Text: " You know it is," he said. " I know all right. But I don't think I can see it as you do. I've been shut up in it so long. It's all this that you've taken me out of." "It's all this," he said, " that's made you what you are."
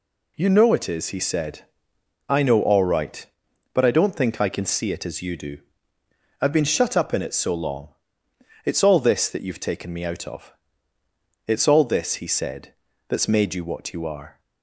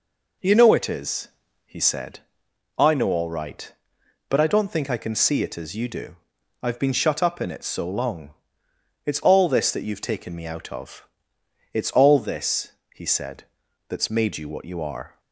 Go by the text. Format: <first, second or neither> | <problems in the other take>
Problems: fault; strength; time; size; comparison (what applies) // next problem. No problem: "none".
neither | none